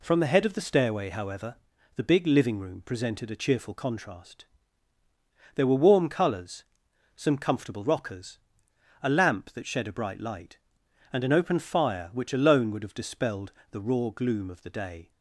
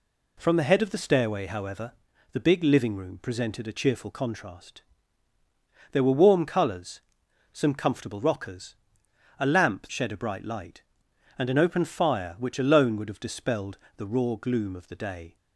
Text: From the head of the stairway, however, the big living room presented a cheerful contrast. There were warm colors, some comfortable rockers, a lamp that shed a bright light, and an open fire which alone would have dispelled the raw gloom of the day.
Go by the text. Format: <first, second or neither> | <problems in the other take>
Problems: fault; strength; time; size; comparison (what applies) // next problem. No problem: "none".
first | skips "that"; at 9.9 s // pauses between "dispelled" and "the"; slight; at 13.7 s; 0.20 s long; slight in the first